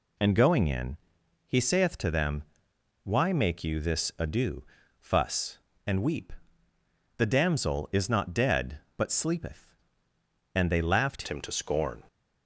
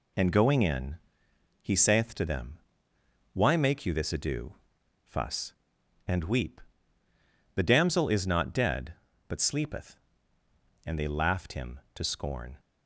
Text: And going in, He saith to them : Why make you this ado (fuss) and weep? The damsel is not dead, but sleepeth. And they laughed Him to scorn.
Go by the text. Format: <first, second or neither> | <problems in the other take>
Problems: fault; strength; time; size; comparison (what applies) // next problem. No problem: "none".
second | changes voice at "Him"; from 11.2 s on; 0.8 s long